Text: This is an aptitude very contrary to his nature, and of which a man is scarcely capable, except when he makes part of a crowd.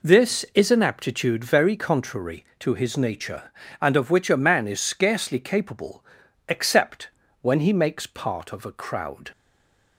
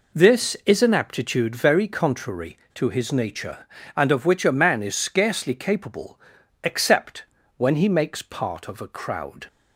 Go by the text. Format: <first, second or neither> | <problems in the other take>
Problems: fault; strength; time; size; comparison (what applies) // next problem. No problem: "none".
second | pauses between "except" and "when"; slight; at 7.0 s; 0.33 s long; slight in the second // stays silent after the last word; slight; from 9.3 s on; 0.6 s long